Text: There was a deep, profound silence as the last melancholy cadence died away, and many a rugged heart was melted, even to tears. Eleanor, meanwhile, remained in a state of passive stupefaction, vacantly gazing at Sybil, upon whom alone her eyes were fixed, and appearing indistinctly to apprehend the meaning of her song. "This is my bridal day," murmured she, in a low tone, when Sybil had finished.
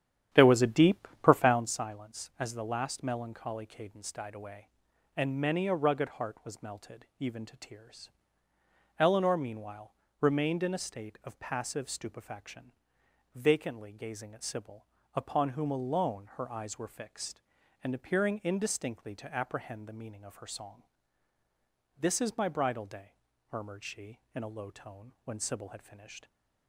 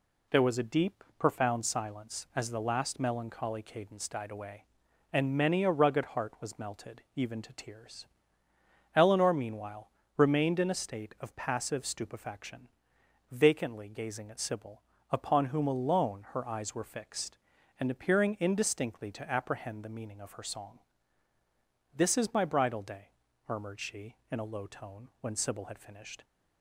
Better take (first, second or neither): second